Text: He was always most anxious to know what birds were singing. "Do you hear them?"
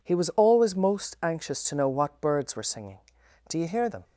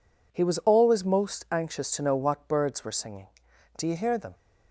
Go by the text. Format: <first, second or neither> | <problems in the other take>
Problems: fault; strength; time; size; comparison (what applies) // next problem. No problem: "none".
neither | none